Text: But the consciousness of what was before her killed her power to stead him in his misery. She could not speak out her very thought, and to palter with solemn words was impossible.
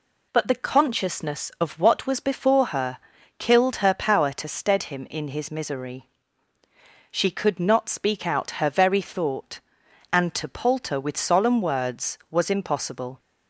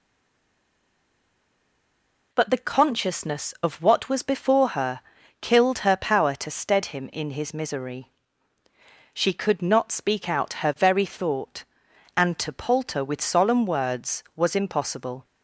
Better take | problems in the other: first | stays silent before the first word; until 2.3 s; 2.3 s long // pauses between "her" and "killed"; at 5.0 s; 0.40 s long; also in the first

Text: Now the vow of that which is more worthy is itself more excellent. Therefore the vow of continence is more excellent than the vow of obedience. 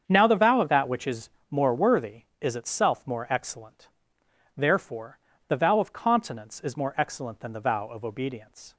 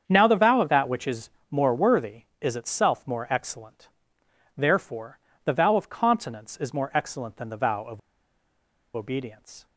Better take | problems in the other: first | starts louder than the rest; strong; until 1.0 s; 7.5 dB; strong in the first // pauses between "is" and "more"; slight; at 1.3 s; 0.18 s long; slight in the first // pauses between "Therefore" and "the"; slight; at 5.1 s; 0.28 s long; slight in the first // pauses between "of" and "obedience"; noticeable; at 7.9 s; 0.97 s long

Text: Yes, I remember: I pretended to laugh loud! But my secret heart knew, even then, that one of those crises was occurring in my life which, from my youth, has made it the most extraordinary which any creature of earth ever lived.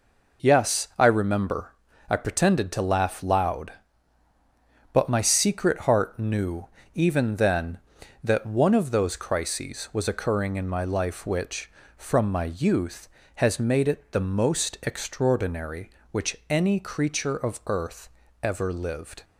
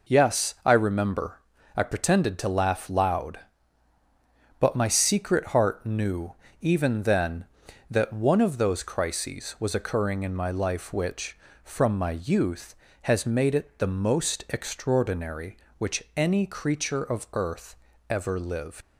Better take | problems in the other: first | pauses between "earth" and "ever"; slight; at 17.7 s; 0.34 s long; slight in the first // leaves "lived" unfinished; at 18.8 s; 85 ms

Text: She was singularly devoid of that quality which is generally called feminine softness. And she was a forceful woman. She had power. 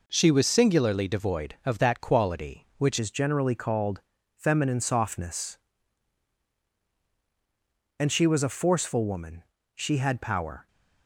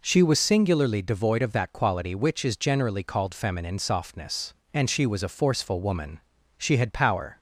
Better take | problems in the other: second | changes voice at "is"; from 2.9 s on; 7.7 s long // pauses between "called" and "feminine"; slight; at 4.0 s; 0.36 s long

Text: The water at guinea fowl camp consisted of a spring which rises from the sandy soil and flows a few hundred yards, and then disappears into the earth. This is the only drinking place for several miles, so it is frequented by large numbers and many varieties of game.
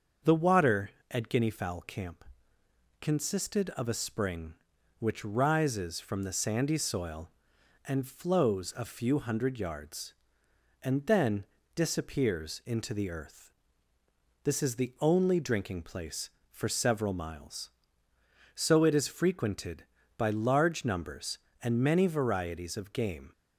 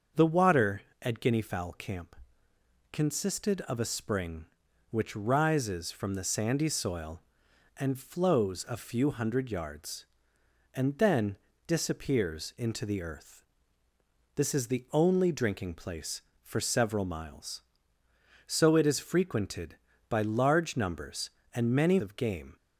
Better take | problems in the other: first | starts louder than the rest; until 1.3 s; 6.5 dB; also in the first // pauses between "camp" and "consisted"; noticeable; at 2.1 s; 0.78 s long; noticeable in the first // pauses between "then" and "disappears"; slight; at 11.3 s; 0.30 s long; slight in the first // skips "varieties"; at 21.9 s

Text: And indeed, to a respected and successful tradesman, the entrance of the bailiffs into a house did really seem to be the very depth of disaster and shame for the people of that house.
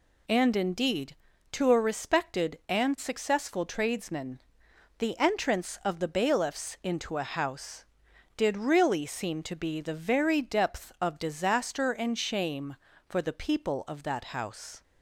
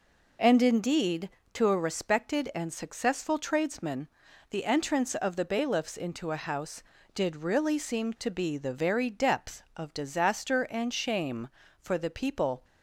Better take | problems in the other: first | stops before "of that house"; at 12.6 s

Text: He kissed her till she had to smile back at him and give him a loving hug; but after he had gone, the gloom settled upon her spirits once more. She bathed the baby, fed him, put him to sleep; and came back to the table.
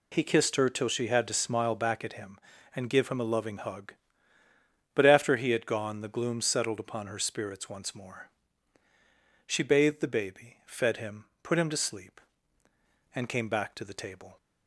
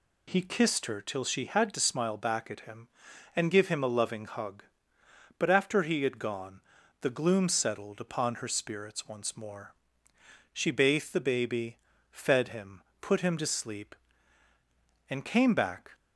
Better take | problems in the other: first | stops before "to the table"; at 15.9 s

